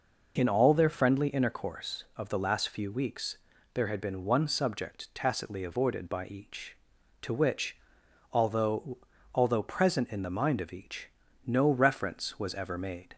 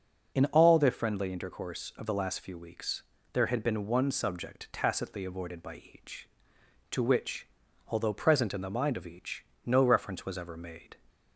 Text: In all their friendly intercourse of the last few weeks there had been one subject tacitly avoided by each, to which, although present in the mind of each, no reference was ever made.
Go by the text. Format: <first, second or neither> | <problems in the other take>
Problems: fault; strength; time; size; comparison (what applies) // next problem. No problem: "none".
second | pauses between "weeks" and "there"; slight; at 3.3 s; 0.34 s long; slight in the second // says "although" twice; at 9.3 s